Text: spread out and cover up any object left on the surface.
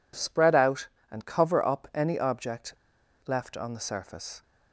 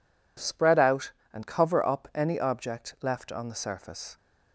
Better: second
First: pauses between "object" and "left"; noticeable; at 2.7 s; 0.51 s long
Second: none

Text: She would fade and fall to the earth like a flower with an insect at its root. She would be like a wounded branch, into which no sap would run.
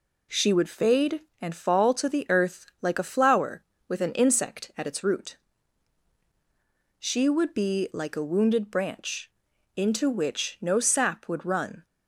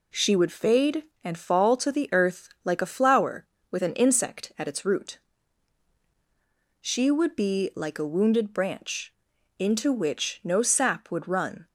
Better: neither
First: none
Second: none

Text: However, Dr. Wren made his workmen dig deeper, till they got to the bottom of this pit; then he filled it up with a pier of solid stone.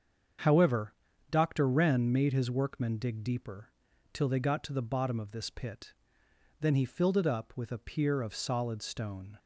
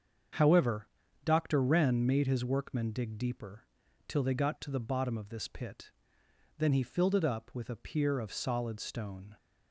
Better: neither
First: starts louder than the rest; until 1.8 s; 7 dB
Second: starts louder than the rest; until 1.7 s; 7 dB

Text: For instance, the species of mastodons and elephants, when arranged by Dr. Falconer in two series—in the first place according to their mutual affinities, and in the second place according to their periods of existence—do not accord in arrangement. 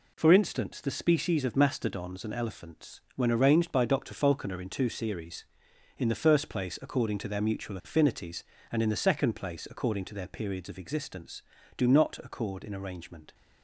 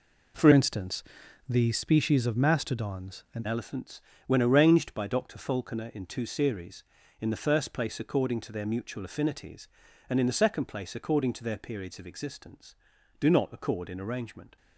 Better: first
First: none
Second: changes voice from "instance" to "and"; from 0.5 to 3.4 s; 2.9 s long

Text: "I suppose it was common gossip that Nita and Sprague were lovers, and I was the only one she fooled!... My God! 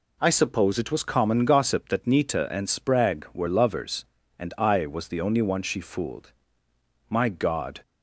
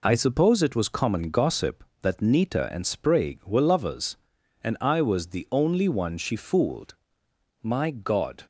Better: neither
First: none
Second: none

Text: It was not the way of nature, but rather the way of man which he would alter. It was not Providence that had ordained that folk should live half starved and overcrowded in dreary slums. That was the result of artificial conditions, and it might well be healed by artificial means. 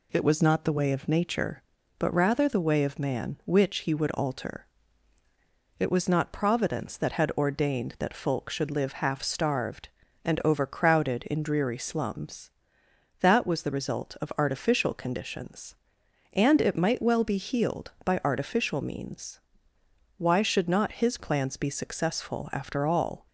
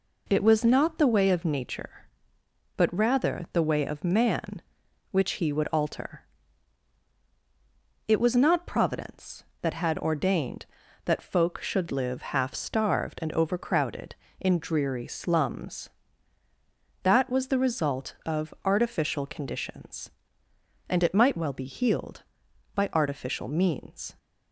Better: second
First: goes on to say "Why should not his plans be successful after all"; strong; from 20.1 s on; 3.1 s long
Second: none

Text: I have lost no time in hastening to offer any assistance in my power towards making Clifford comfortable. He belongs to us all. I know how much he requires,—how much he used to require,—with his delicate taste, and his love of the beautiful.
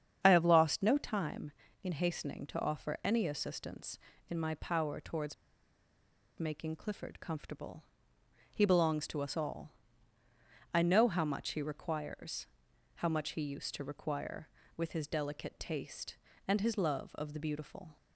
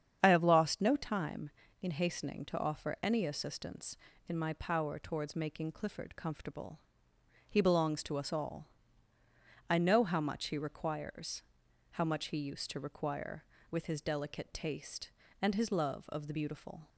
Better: second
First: starts louder than the rest; strong; until 1.2 s; 8 dB // pauses between "towards" and "making"; at 5.3 s; 1.0 s long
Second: starts louder than the rest; strong; until 1.2 s; 8 dB

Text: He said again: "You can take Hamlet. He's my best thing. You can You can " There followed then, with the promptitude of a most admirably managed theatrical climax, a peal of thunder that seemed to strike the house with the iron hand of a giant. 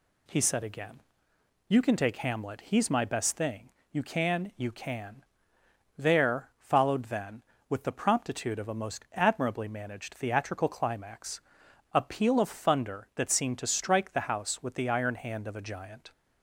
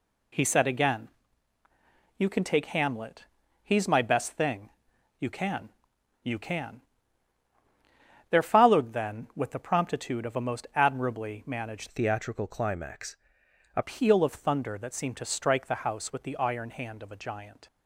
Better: first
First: none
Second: pauses between "can" and "You"; noticeable; at 5.6 s; 0.54 s long // changes voice from "theatrical" to "a"; from 11.8 to 13.8 s; 2.0 s long

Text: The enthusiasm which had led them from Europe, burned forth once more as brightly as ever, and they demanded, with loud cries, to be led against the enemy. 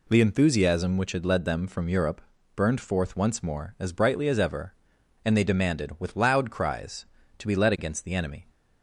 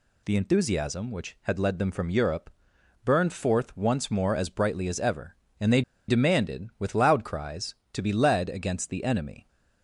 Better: first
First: none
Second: pauses between "they" and "demanded"; slight; at 5.8 s; 0.27 s long

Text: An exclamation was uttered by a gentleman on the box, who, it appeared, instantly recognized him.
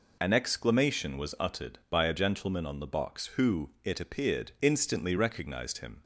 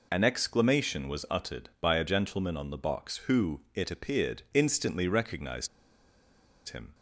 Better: first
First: none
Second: pauses between "recognized" and "him"; at 5.6 s; 1.0 s long

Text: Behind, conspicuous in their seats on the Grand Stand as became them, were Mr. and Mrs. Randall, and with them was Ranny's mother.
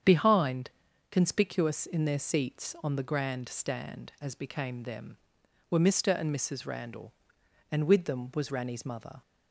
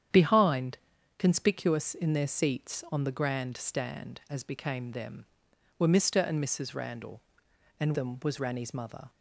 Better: first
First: starts louder than the rest; strong; until 1.4 s; 8 dB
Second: starts louder than the rest; strong; until 1.5 s; 9 dB // skips "with"; at 7.9 s

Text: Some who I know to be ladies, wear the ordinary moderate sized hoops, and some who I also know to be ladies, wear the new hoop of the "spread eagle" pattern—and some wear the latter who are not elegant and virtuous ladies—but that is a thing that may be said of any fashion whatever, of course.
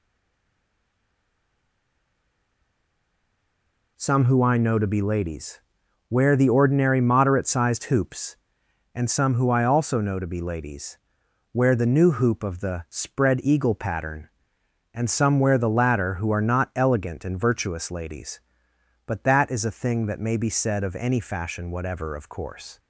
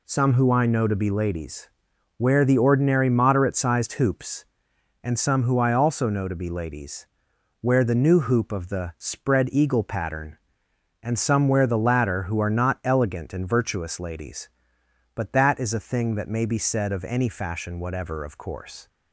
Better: second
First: stays silent before the first word; strong; until 3.9 s; 3.9 s long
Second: none

